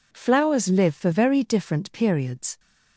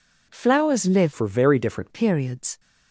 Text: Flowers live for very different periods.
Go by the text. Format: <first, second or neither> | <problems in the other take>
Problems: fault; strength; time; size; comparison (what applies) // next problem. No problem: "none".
first | changes voice from "for" to "different"; from 1.1 to 1.8 s; 0.7 s long